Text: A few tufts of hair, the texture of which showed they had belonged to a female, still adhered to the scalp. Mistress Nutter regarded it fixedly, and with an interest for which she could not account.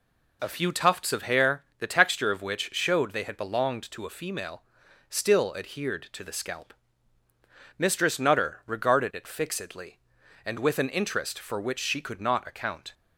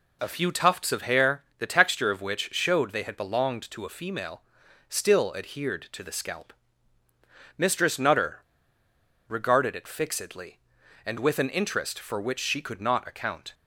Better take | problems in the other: first | pauses between "Nutter" and "regarded"; noticeable; at 8.4 s; 0.86 s long

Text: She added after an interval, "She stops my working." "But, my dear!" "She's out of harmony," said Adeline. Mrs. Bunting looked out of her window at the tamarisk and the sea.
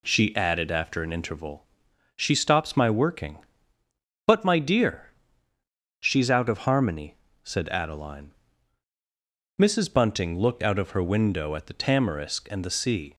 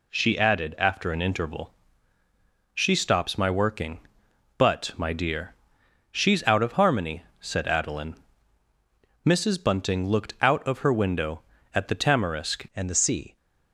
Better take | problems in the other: first | changes voice at "and"; from 12.7 s on; 0.6 s long

